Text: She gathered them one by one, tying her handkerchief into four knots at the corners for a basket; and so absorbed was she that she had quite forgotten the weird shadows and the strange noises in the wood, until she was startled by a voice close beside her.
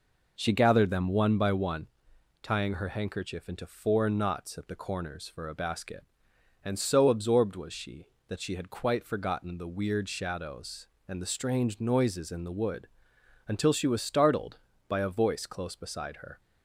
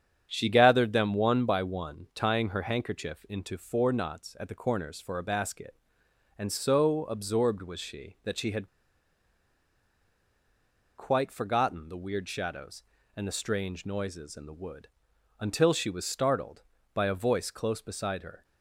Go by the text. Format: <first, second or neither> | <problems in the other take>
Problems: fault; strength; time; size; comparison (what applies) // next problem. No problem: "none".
first | starts louder than the rest; strong; until 1.3 s; 8.5 dB // pauses between "had" and "quite"; strong; at 8.6 s; 2.3 s long